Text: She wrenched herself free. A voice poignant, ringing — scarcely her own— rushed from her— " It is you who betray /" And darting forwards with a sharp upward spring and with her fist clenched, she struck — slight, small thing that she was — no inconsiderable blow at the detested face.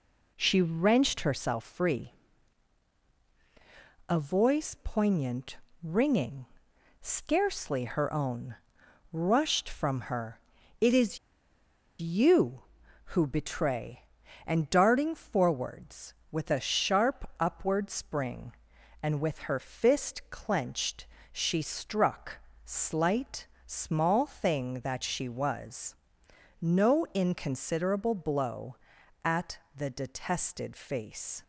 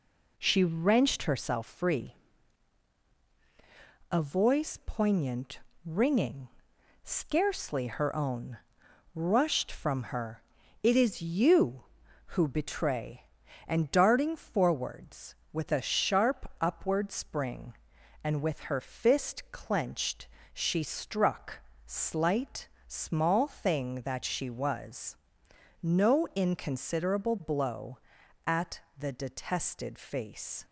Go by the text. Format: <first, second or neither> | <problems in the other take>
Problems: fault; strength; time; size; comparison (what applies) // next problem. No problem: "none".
second | pauses between "is" and "you"; noticeable; at 11.1 s; 0.82 s long // pauses between "at" and "the"; slight; at 29.5 s; 0.18 s long; slight in the second